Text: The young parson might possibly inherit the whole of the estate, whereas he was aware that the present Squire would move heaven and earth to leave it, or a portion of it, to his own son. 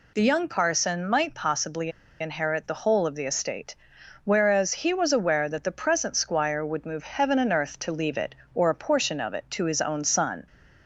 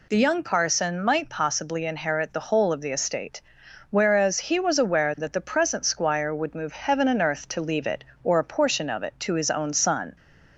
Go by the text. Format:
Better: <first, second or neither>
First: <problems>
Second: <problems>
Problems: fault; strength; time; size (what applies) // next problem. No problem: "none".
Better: second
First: pauses between "possibly" and "inherit"; slight; at 1.9 s; 0.29 s long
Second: none